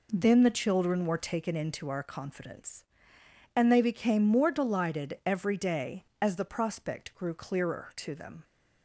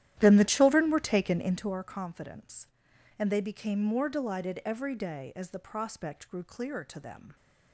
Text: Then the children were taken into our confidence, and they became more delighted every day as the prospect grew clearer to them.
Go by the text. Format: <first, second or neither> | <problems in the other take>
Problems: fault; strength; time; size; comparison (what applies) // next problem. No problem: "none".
first | starts louder than the rest; strong; until 1.8 s; 12 dB